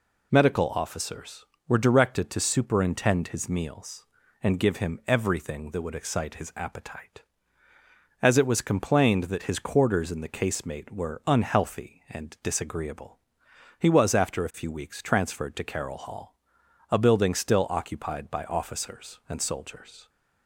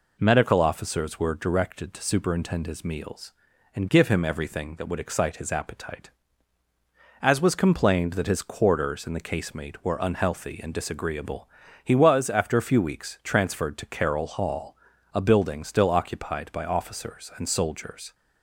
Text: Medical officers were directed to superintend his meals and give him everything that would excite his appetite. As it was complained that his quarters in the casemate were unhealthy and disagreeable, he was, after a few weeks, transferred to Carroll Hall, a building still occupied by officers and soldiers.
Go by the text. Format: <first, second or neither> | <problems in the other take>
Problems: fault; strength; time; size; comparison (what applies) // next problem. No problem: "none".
first | skips "it"; at 7.4 s